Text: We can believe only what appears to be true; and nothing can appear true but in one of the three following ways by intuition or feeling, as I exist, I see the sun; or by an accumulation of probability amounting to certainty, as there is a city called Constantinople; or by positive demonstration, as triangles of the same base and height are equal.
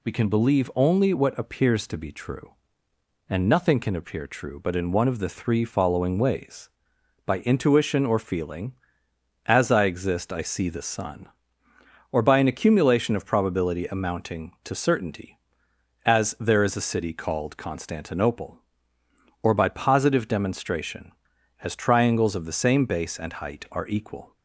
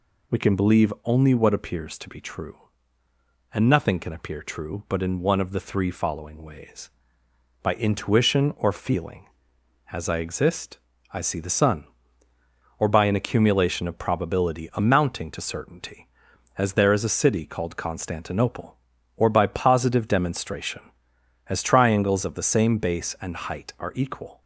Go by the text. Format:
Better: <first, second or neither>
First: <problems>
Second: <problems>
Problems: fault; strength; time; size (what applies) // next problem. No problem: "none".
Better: neither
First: none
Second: none